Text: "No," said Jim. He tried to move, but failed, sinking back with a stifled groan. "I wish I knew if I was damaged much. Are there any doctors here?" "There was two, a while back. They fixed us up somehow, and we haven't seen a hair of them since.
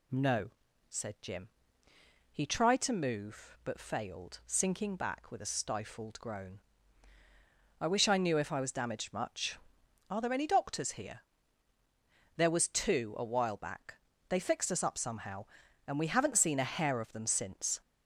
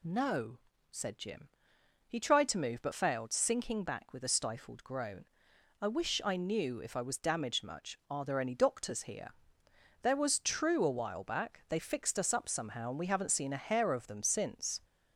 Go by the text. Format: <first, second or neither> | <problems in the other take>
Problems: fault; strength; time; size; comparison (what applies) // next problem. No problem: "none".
first | says "true" for "two"; at 10.3 s